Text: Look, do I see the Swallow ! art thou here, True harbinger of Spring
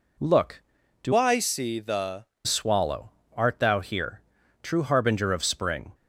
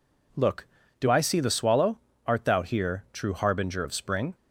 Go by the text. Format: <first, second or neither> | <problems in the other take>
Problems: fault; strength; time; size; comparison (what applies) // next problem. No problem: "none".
second | changes voice from "I" to "the"; from 1.1 to 2.2 s; 1.1 s long